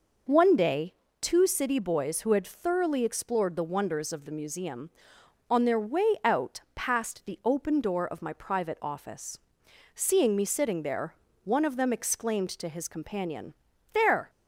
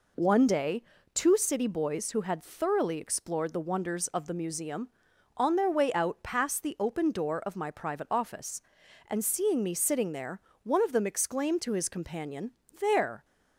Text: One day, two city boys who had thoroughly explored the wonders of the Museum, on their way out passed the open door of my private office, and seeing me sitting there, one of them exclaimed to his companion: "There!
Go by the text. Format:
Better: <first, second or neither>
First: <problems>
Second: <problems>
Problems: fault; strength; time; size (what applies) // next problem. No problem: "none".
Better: second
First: pauses between "out" and "passed"; slight; at 6.5 s; 0.16 s long // skips "and"; at 9.6 s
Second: none